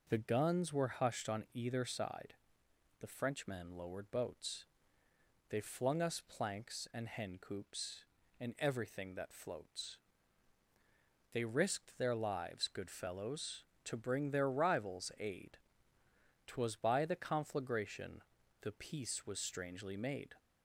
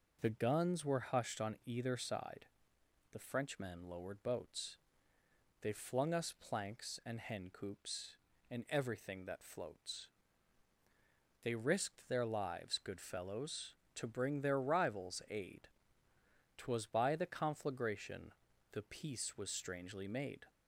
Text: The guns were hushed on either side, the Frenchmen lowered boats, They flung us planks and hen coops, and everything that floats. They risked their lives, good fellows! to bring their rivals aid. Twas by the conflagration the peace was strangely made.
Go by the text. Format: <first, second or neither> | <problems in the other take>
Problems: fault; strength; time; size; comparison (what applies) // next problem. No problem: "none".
neither | pauses between "conflagration" and "the"; the same in both